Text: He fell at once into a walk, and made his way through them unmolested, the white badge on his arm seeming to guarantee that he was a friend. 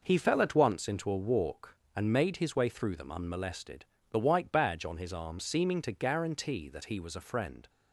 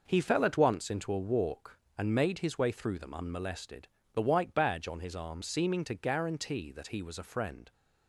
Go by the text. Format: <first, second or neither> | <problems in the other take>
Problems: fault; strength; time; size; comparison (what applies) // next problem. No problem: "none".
neither | none